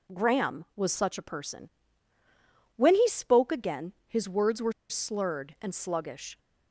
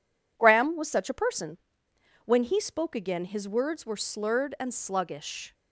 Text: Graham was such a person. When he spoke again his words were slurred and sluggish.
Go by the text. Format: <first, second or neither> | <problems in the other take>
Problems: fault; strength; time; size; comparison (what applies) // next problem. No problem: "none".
second | pauses between "were" and "slurred"; slight; at 4.7 s; 0.17 s long